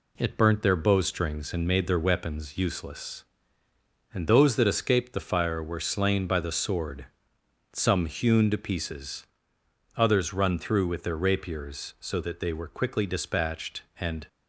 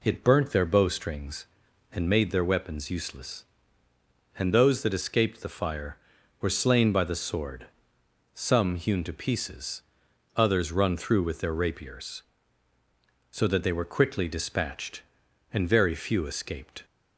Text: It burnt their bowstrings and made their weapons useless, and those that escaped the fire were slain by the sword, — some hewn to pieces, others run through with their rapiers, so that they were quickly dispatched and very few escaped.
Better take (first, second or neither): second